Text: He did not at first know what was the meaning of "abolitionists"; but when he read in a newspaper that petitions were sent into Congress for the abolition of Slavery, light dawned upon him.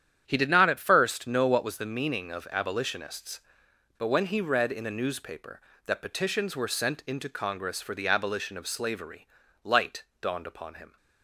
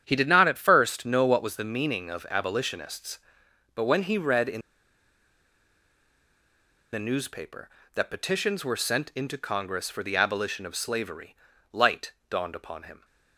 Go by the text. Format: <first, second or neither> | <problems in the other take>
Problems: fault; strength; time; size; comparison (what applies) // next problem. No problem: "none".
first | starts louder than the rest; strong; until 1.0 s; 9 dB; strong in the first // pauses between "in" and "a"; strong; at 4.6 s; 2.3 s long // pauses between "light" and "dawned"; slight; at 12.1 s; 0.18 s long; slight in the first